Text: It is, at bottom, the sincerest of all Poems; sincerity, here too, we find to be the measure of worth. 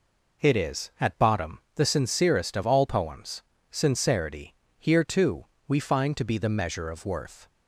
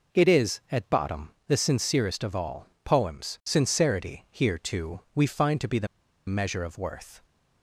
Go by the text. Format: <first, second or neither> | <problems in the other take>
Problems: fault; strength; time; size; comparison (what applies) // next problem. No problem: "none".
first | pauses between "all" and "Poems"; slight; at 2.6 s; 0.16 s long // pauses between "the" and "measure"; at 5.8 s; 0.41 s long